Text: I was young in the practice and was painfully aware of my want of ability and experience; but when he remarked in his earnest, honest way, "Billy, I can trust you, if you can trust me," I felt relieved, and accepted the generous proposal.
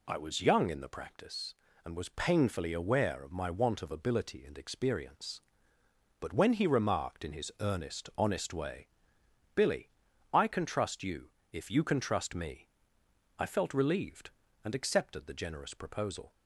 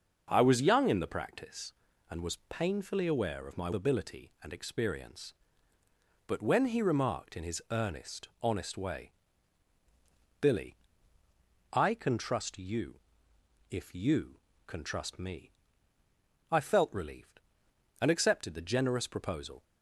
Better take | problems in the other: first | skips "want of"; at 3.7 s

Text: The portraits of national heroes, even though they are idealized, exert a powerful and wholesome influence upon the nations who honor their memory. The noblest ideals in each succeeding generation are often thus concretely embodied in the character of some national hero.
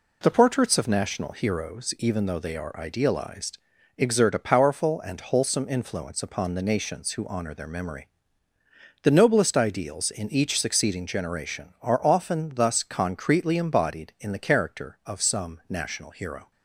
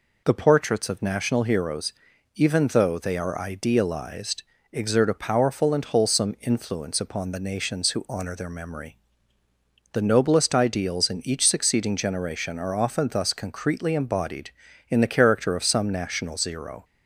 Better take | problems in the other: first | says "zero" for "hero"; at 16.3 s

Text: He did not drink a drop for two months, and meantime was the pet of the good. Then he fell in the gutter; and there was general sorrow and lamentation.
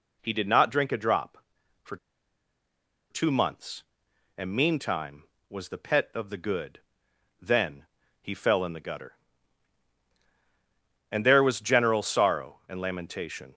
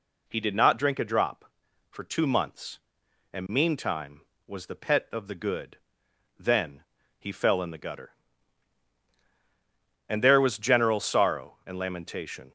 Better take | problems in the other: second | pauses between "for" and "two"; at 1.9 s; 1.1 s long // pauses between "Then" and "he"; slight; at 7.8 s; 0.34 s long; slight in the second

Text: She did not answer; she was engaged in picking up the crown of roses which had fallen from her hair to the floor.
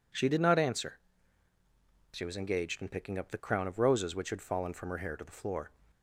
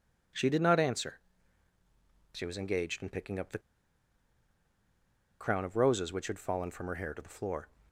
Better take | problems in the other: first | pauses between "the" and "crown"; strong; at 3.6 s; 1.8 s long

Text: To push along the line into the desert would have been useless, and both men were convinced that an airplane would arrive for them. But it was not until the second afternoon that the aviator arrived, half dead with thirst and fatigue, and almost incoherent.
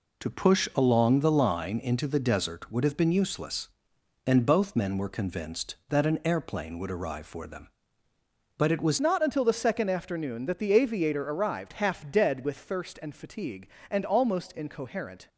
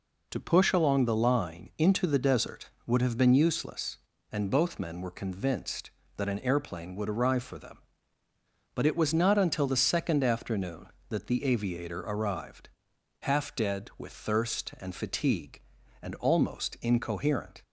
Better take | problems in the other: second | changes voice at "not"; from 9.0 s on; 6.2 s long

